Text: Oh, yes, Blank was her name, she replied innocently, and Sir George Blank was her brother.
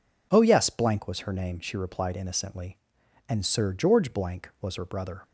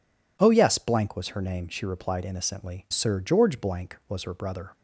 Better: first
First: none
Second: skips "and"; at 2.8 s

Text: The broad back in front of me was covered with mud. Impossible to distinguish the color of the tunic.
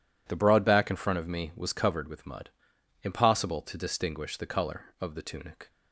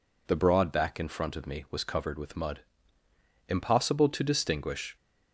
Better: first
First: none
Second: stops before "the color of the tunic"; at 4.9 s

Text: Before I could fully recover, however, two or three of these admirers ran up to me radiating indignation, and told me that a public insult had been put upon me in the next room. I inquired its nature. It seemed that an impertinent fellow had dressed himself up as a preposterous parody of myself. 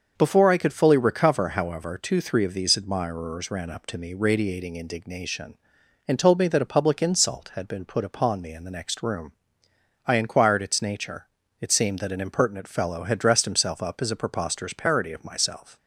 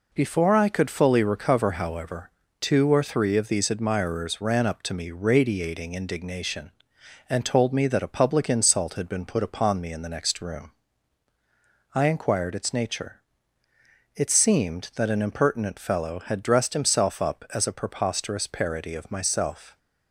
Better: second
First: starts louder than the rest; until 1.1 s; 6.5 dB // skips "or"; at 2.2 s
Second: none

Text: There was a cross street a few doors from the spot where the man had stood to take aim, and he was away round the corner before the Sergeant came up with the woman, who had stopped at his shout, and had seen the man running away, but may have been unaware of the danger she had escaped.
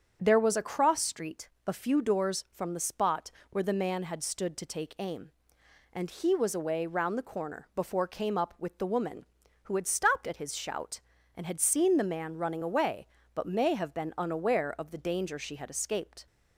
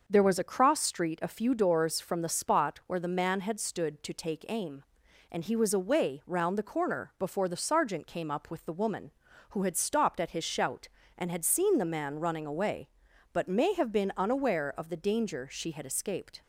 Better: second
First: starts louder than the rest; strong; until 1.2 s; 7.5 dB // pauses between "street" and "a"; slight; at 1.4 s; 0.16 s long // pauses between "spot" and "where"; slight; at 3.3 s; 0.22 s long // skips "the Sergeant"; at 8.0 s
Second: starts louder than the rest; until 1.0 s; 6.5 dB

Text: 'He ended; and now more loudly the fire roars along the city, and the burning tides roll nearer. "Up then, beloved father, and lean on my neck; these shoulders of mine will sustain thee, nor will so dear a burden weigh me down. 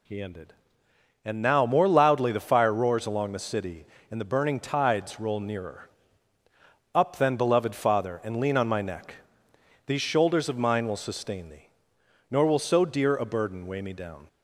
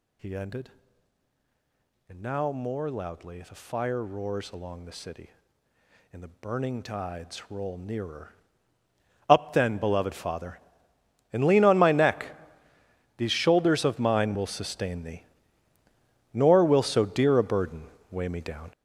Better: first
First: none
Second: gets louder; strong; throughout; 11 dB // pauses between "burden" and "weigh"; slight; at 17.8 s; 0.26 s long

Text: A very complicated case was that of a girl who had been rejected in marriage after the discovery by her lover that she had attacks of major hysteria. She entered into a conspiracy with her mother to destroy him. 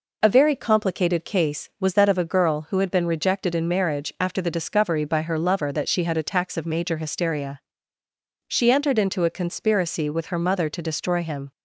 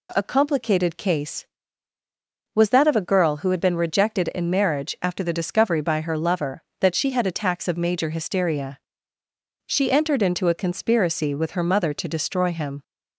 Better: first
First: none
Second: skips "very"; at 0.2 s

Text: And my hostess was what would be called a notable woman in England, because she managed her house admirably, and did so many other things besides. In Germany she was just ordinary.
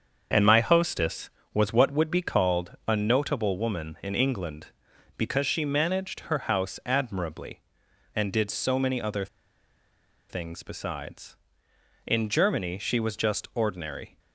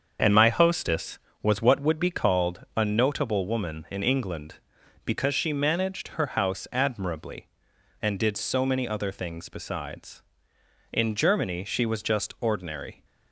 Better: second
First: starts louder than the rest; until 1.5 s; 6.5 dB // pauses between "other" and "things"; at 9.2 s; 1.0 s long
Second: starts louder than the rest; until 1.4 s; 6.5 dB

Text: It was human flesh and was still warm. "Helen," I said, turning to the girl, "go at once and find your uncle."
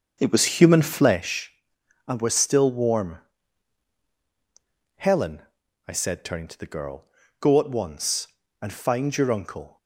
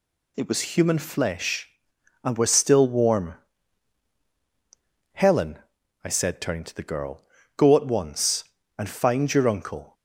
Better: second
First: starts louder than the rest; until 1.3 s; 6.5 dB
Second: none

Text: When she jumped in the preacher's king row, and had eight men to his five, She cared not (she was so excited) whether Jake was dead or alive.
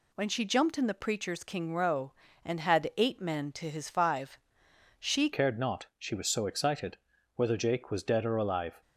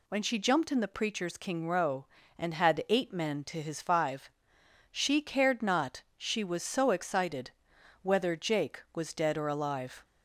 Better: second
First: changes voice at "cared"; from 5.3 s on; 3.5 s long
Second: none

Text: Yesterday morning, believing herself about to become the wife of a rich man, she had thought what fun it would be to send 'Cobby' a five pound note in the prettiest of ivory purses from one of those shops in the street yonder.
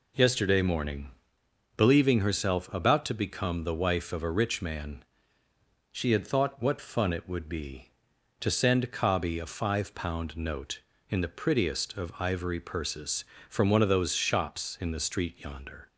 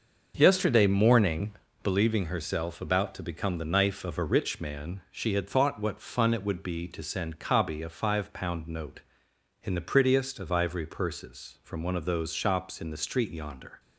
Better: first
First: none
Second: starts louder than the rest; until 1.3 s; 6 dB // says "knife" for "wife"; at 3.6 s

